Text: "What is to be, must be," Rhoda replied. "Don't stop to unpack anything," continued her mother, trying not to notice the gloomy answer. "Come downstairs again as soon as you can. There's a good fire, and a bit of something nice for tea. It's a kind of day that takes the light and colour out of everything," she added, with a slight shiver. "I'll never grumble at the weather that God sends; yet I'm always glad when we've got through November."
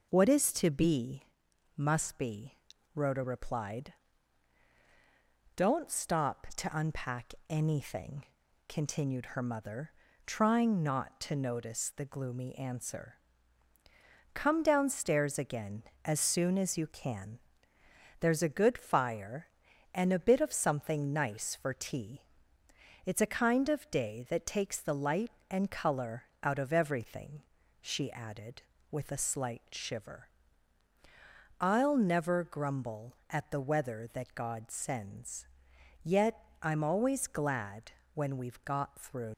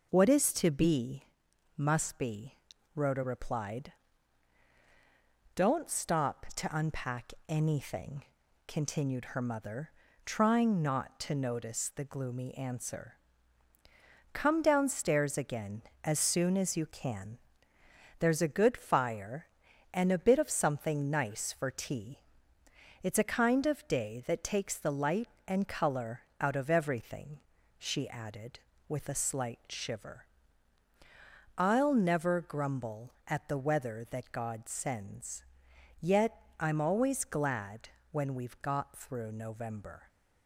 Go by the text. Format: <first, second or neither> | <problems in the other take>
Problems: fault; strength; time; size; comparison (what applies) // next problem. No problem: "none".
second | pauses between "colour" and "out"; slight; at 26.2 s; 0.18 s long; slight in the second // pauses between "yet" and "I'm"; slight; at 36.4 s; 0.20 s long; slight in the second // pauses between "glad" and "when"; slight; at 37.9 s; 0.24 s long; slight in the second // stops before "November"; at 39.3 s